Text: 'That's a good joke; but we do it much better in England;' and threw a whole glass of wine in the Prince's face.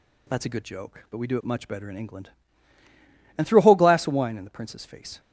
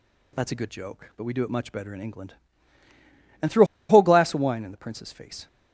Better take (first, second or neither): first